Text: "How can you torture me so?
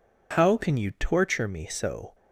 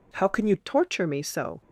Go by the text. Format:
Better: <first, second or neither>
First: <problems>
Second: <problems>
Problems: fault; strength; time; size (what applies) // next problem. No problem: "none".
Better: first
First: none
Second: changes voice at "torture"; from 0.5 s on; 1.1 s long